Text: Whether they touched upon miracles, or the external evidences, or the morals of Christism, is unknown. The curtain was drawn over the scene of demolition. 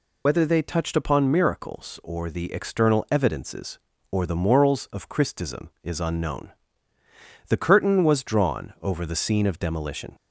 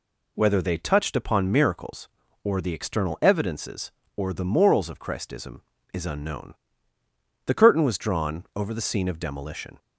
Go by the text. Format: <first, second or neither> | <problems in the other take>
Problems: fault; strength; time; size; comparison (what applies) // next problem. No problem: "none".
second | loses the start of "Whether"; at 0.2 s; 65 ms